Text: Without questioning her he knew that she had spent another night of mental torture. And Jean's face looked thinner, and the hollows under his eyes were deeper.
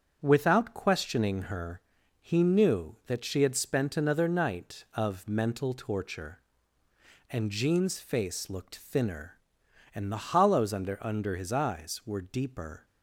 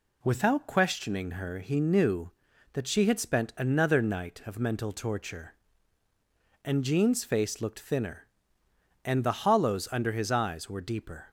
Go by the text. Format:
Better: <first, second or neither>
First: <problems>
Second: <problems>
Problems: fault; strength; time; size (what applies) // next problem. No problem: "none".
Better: second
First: starts louder than the rest; strong; until 1.2 s; 7.5 dB // pauses between "her" and "he"; at 1.8 s; 0.40 s long // says "under" twice; at 11.0 s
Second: none